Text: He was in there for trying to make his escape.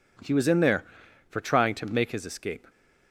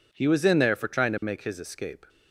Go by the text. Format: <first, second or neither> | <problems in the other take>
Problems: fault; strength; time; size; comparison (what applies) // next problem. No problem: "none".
neither | none